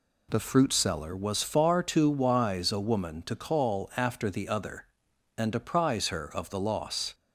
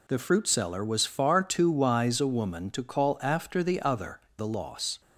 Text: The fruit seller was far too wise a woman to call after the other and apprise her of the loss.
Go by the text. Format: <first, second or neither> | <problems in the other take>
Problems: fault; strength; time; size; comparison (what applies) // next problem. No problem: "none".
first | skips "and apprise her of"; at 4.2 s